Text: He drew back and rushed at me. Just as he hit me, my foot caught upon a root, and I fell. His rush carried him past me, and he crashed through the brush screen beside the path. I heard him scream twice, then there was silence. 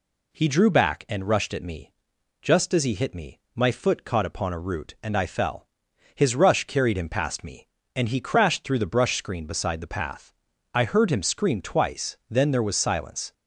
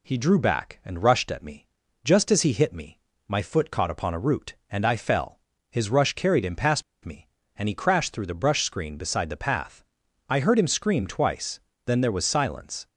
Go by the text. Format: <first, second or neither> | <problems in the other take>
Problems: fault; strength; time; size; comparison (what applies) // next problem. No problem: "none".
first | pauses between "past" and "me"; slight; at 6.8 s; 0.22 s long